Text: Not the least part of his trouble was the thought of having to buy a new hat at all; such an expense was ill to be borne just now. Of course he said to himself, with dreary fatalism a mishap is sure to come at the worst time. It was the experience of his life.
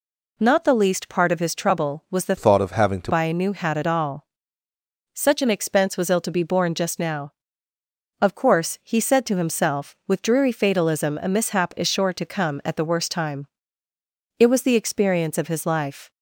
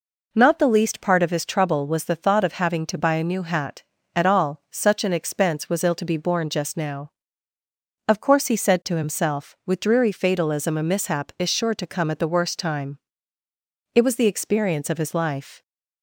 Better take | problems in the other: second | changes voice from "thought" to "to"; from 2.3 to 3.1 s; 0.8 s long

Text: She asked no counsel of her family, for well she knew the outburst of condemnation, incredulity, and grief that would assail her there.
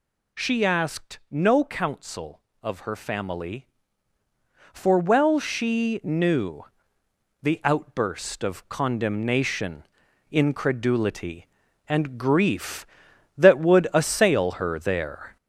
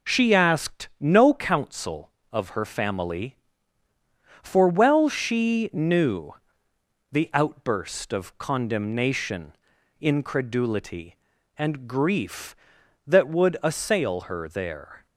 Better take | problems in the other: second | gets louder; noticeable; throughout; 4.5 dB // pauses between "knew" and "the"; noticeable; at 6.6 s; 0.76 s long; noticeable in the second

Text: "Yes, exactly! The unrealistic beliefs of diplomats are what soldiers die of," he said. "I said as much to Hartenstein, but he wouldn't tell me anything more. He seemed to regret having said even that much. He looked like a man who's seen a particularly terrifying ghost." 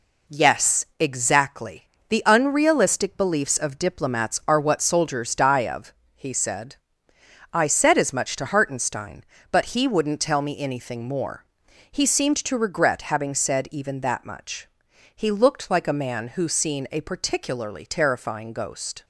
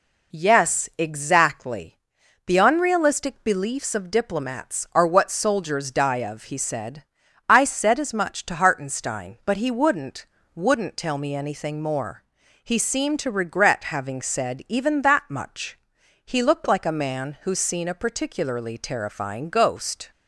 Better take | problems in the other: first | says "wouldn't" twice; at 10.5 s

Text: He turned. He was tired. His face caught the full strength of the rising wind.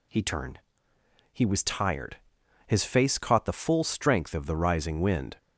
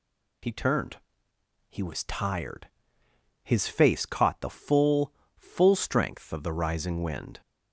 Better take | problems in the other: first | says "full" twice; at 5.3 s

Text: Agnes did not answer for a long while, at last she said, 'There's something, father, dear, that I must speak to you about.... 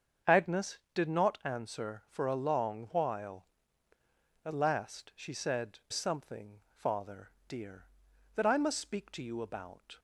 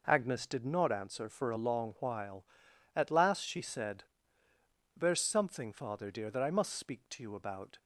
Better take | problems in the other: second | starts louder than the rest; until 1.4 s; 7 dB // skips "There's"; at 5.8 s

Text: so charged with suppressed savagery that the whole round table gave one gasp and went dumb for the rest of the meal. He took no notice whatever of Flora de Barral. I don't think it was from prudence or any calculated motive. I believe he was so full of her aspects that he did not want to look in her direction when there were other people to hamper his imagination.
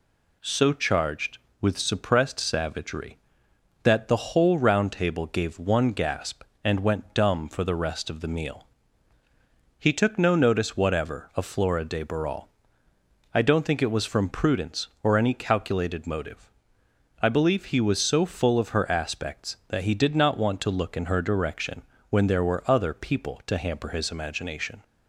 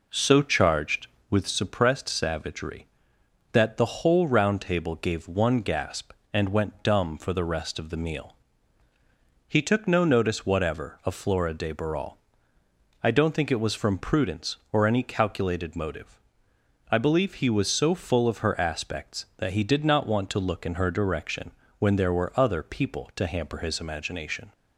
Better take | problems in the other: first | starts louder than the rest; noticeable; until 1.5 s; 4.5 dB // pauses between "direction" and "when"; slight; at 21.5 s; 0.26 s long; slight in the first

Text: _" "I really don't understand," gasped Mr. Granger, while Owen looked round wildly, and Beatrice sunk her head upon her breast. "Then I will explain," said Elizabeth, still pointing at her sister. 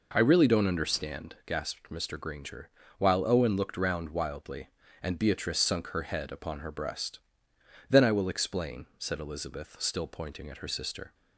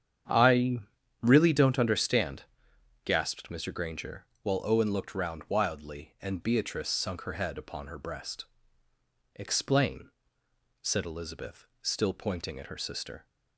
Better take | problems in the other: first | starts louder than the rest; strong; until 1.6 s; 8.5 dB // pauses between "I" and "really"; at 0.8 s; 0.42 s long // skips "Then I will"; at 8.9 s

